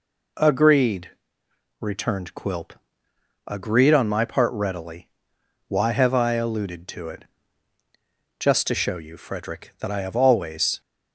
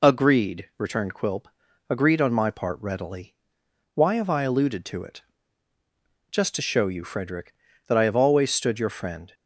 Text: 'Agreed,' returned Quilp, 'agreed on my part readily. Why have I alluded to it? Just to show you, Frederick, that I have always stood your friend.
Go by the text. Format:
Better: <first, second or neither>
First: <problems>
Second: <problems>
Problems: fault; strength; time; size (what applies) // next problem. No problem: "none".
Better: second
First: stops before "stood your friend"; at 10.8 s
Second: none